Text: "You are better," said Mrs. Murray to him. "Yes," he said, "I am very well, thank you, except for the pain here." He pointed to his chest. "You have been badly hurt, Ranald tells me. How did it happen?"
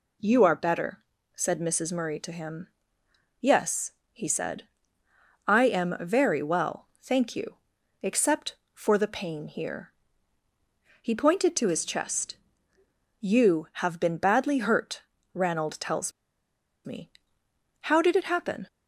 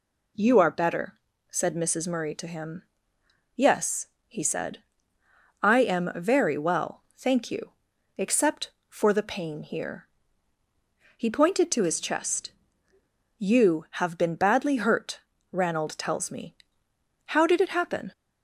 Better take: second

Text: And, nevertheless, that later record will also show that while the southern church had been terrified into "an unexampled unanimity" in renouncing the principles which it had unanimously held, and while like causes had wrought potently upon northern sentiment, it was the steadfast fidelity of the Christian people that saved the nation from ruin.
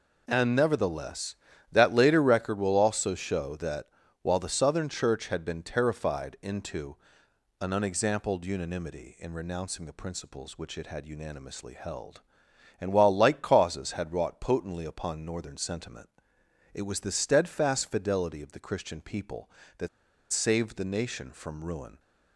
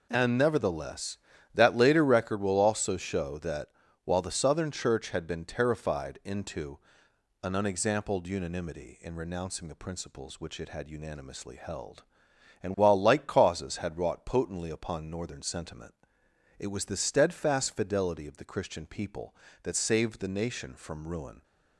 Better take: second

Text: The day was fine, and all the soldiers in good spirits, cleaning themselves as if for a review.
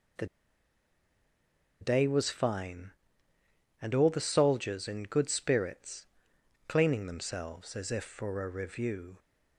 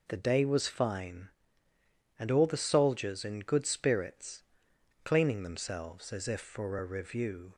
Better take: second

